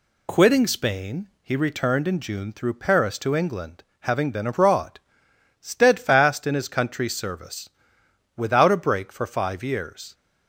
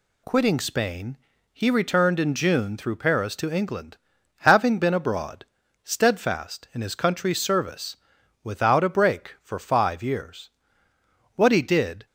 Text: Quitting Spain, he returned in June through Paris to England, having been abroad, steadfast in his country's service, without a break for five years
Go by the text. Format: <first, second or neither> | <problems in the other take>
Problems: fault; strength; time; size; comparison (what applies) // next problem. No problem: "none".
first | goes on to say "What he did"; noticeable; from 11.3 s on; 0.70 s long